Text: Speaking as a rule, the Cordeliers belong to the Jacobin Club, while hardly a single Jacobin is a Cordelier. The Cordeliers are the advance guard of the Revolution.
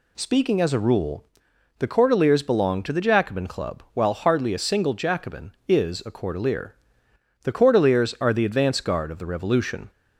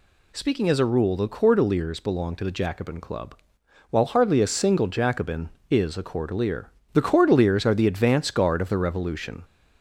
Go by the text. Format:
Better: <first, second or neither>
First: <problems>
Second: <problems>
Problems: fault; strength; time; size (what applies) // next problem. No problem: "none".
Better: neither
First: none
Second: none